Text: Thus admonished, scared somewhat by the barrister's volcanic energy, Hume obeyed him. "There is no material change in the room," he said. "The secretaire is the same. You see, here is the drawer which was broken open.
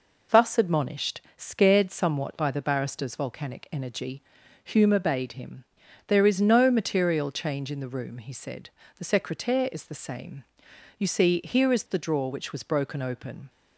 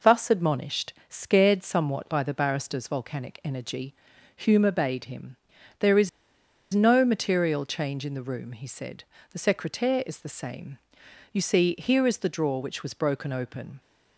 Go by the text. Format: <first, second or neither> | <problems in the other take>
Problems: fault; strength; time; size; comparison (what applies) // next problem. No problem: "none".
first | pauses between "is" and "no"; noticeable; at 6.0 s; 0.64 s long